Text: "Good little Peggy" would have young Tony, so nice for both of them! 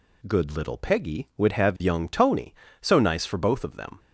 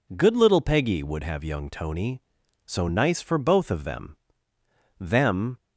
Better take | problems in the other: first | says "them" twice; at 5.0 s

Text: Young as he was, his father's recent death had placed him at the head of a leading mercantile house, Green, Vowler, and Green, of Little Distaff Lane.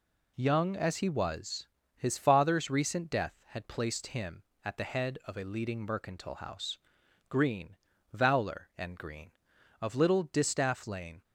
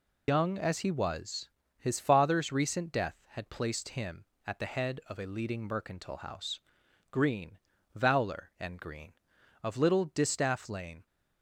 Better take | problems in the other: first | loses the start of "Young"; at 0.2 s; 105 ms

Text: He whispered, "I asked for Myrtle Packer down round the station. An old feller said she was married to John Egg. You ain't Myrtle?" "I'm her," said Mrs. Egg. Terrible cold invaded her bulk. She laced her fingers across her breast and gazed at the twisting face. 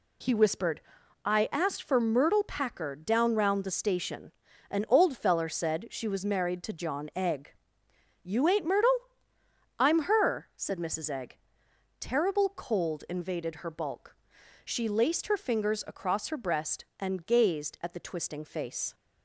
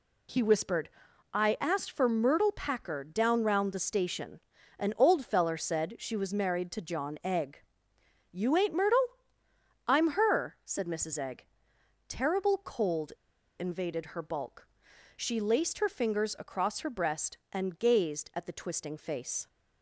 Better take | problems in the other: first | pauses between "cold" and "invaded"; noticeable; at 13.1 s; 0.48 s long

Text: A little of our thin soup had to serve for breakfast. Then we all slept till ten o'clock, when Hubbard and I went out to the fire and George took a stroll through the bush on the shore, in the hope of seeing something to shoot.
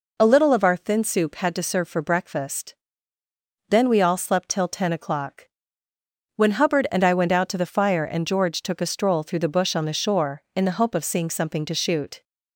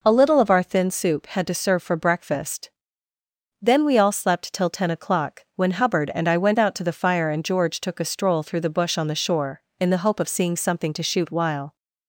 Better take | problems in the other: first | goes on to say "While"; slight; from 11.2 s on; 0.46 s long

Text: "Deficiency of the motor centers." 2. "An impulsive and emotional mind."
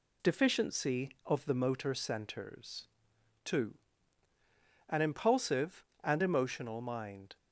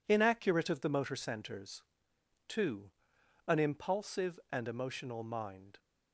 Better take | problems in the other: first | says "Inaccurate" for "Deficiency"; at 0.0 s

